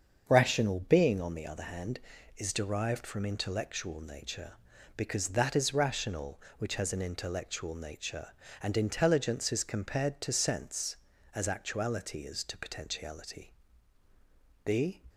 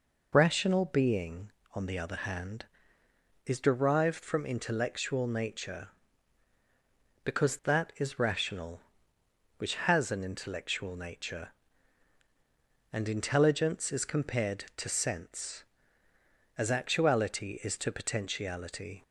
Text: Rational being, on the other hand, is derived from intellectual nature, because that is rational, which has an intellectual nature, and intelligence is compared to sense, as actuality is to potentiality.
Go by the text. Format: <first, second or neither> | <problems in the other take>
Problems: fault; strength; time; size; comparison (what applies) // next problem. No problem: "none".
second | starts louder than the rest; until 1.2 s; 7 dB // goes on to say "The"; slight; from 14.6 s on; 0.40 s long